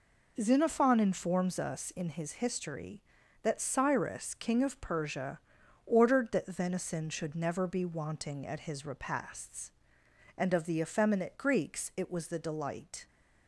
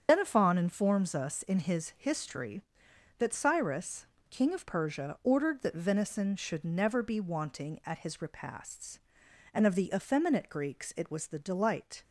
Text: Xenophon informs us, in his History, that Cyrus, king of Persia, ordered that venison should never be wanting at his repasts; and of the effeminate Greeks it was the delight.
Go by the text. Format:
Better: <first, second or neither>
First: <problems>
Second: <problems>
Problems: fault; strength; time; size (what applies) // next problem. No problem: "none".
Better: first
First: none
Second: loses the start of "Xenophon"; at 0.0 s; 75 ms // starts louder than the rest; strong; until 1.1 s; 7.5 dB